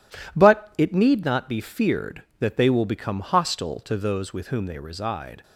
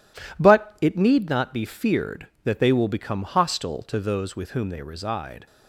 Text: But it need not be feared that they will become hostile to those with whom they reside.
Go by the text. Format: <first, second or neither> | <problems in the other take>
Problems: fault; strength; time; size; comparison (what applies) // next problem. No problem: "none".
neither | none